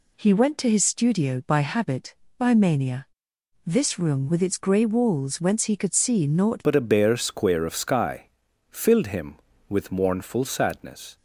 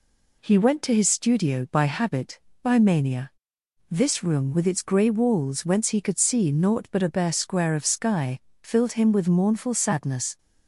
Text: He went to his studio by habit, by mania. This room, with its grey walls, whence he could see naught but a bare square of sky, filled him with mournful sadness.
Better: second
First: changes voice at "but"; from 6.6 s on; 4.5 s long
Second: none

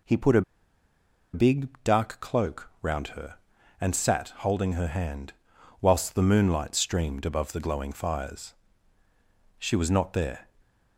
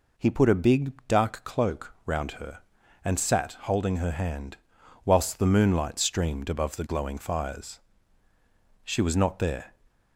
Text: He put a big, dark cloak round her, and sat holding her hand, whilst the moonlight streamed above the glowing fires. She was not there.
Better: second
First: pauses between "a" and "big"; noticeable; at 0.4 s; 0.92 s long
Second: none

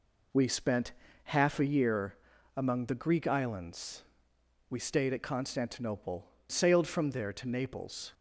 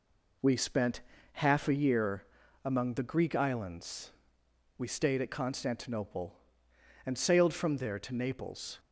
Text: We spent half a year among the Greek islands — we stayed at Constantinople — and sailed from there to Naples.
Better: second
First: pauses between "spent" and "half"; slight; at 0.9 s; 0.32 s long // pauses between "year" and "among"; at 2.1 s; 0.40 s long // skips "and"; at 6.3 s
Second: pauses between "spent" and "half"; slight; at 1.0 s; 0.32 s long // pauses between "year" and "among"; at 2.2 s; 0.39 s long

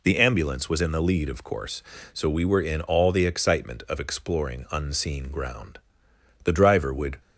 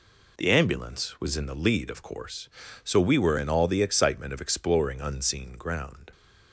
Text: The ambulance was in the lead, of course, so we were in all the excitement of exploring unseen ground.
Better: second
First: goes on to say "The driver would"; noticeable; from 6.4 s on; 0.74 s long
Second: none

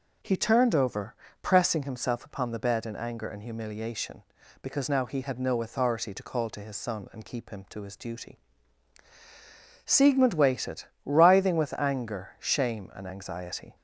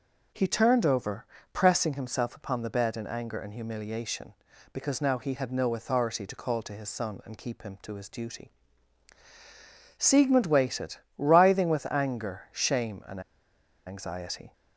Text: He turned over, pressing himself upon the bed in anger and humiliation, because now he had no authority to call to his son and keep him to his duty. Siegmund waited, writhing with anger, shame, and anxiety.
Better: first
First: none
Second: pauses between "and" and "anxiety"; noticeable; at 13.2 s; 0.66 s long

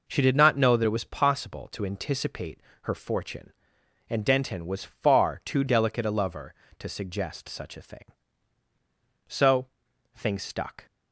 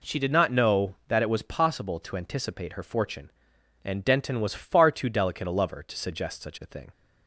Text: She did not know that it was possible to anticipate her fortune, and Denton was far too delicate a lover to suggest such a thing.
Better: second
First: pauses between "anticipate" and "her"; slight; at 2.6 s; 0.22 s long // goes on to say "So things stuck"; from 9.2 s on; 1.5 s long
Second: none

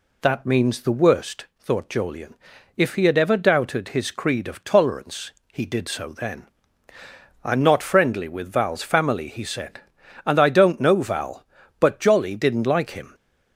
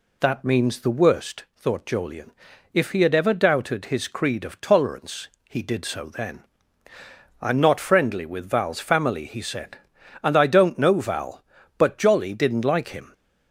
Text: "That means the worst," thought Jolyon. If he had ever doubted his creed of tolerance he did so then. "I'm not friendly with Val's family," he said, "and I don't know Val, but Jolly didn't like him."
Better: neither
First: pauses between "tolerance" and "he"; slight; at 5.3 s; 0.22 s long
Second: pauses between "tolerance" and "he"; slight; at 5.2 s; 0.22 s long

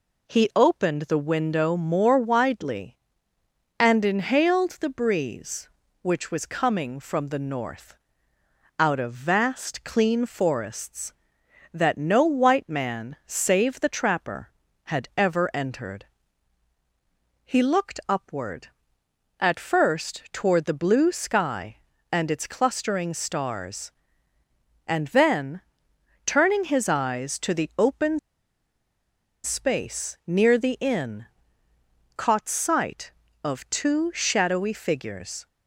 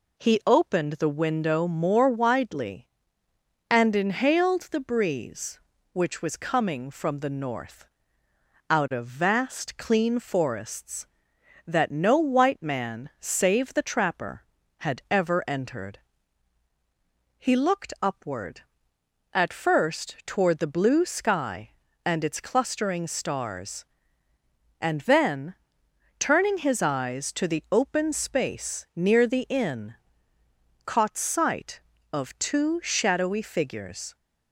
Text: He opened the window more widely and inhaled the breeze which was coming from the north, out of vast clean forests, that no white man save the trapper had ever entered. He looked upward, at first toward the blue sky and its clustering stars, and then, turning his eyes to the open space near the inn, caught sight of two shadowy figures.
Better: second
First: pauses between "open" and "space"; strong; at 28.1 s; 1.2 s long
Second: none

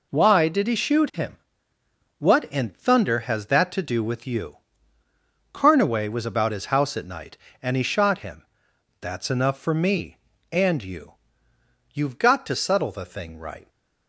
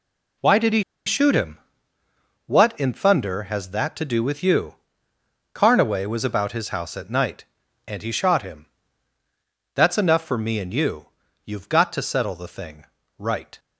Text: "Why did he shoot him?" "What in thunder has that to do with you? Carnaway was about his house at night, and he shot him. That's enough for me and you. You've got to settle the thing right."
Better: first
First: none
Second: pauses between "he" and "shoot"; slight; at 0.8 s; 0.23 s long // pauses between "thing" and "right"; slight; at 12.8 s; 0.32 s long

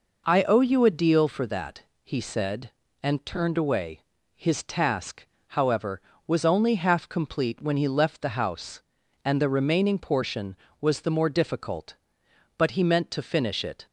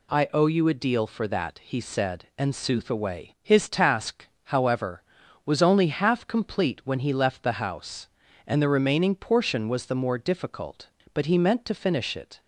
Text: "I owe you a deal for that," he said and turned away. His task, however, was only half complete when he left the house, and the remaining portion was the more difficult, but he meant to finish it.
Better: first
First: none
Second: says "sooth" for "turned"; at 2.5 s

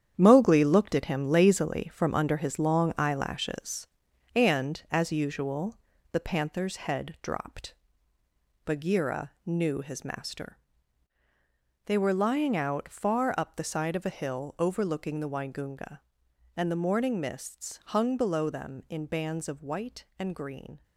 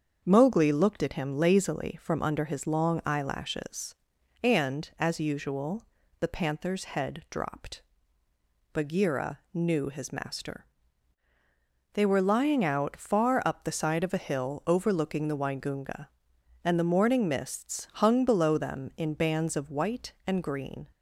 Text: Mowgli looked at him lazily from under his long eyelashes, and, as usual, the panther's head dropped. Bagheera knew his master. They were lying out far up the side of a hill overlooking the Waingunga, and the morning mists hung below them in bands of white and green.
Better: second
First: gets quieter; strong; throughout; 8.5 dB // starts louder than the rest; strong; until 1.1 s; 9 dB // pauses between "Bagheera" and "knew"; slight; at 9.3 s; 0.16 s long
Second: starts louder than the rest; until 1.2 s; 7 dB // pauses between "Bagheera" and "knew"; slight; at 9.3 s; 0.16 s long

